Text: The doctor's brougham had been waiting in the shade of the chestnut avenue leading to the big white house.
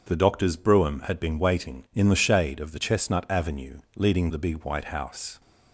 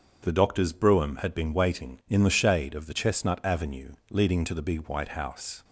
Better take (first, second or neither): second